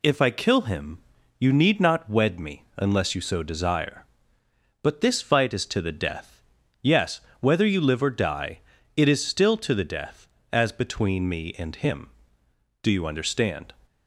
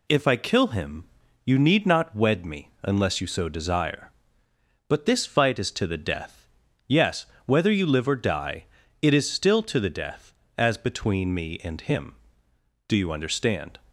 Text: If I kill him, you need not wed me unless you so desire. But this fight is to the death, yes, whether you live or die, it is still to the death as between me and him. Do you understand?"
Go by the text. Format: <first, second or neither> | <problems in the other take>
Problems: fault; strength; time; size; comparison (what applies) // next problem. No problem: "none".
neither | none